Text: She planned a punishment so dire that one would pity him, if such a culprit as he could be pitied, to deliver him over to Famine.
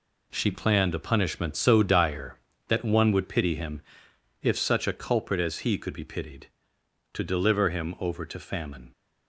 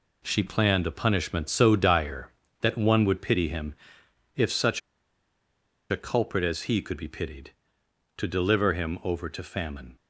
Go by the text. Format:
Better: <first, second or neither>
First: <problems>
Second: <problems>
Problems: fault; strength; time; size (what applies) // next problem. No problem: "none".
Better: first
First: none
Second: pauses between "such" and "a"; at 4.7 s; 1.1 s long